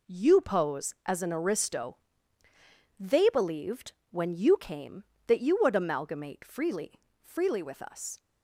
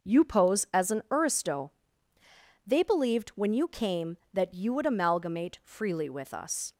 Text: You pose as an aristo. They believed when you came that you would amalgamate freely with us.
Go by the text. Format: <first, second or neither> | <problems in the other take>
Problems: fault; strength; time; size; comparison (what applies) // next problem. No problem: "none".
second | pauses between "believed" and "when"; slight; at 3.9 s; 0.18 s long // says "freely" twice; at 7.2 s